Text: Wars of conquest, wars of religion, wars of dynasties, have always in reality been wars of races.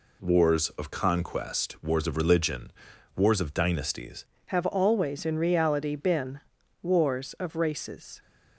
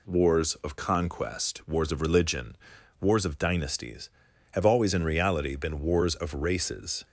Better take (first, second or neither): second